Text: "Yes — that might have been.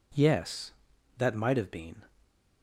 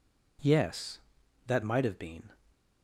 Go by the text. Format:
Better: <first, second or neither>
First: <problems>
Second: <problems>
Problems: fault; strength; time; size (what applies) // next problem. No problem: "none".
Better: neither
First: none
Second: none